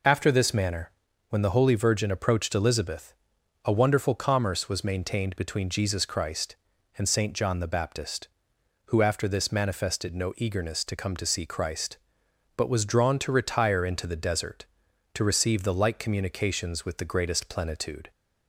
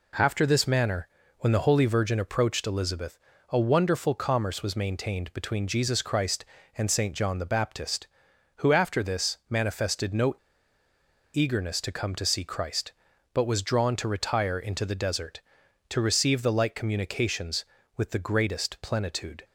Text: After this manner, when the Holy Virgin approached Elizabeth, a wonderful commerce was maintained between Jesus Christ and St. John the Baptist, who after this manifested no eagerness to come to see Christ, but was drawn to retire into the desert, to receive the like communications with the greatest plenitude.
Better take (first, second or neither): first